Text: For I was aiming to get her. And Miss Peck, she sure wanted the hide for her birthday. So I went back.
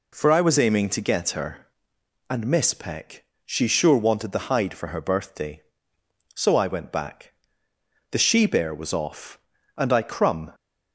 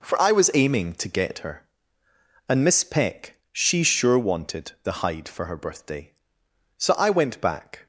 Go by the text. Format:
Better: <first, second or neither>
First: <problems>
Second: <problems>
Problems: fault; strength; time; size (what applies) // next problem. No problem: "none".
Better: second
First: goes on to say "The she bear was off and I crumb"; strong; from 8.1 s on; 2.4 s long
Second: none